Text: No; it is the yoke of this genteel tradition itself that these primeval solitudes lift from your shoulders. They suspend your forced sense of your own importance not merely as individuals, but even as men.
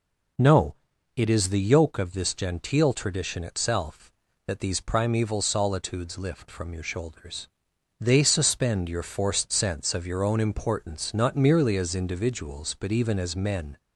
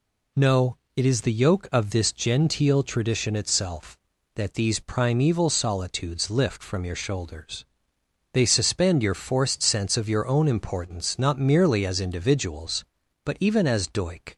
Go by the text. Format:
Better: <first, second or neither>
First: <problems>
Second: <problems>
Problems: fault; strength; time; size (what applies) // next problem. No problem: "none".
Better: first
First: none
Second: says "doik" for "men"; at 13.8 s